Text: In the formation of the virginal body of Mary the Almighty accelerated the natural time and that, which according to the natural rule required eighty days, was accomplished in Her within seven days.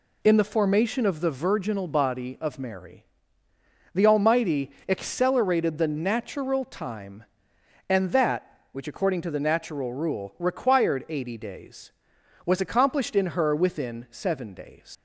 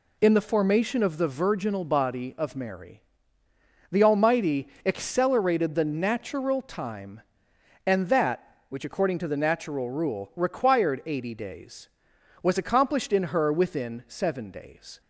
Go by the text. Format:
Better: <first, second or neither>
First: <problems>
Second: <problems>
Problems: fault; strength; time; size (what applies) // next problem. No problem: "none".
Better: second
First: pauses between "Mary" and "the"; noticeable; at 3.0 s; 0.88 s long // pauses between "Almighty" and "accelerated"; slight; at 4.7 s; 0.16 s long // leaves "days" unfinished; at 14.9 s; 80 ms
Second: pauses between "Mary" and "the"; noticeable; at 3.0 s; 0.88 s long // pauses between "Almighty" and "accelerated"; slight; at 4.6 s; 0.16 s long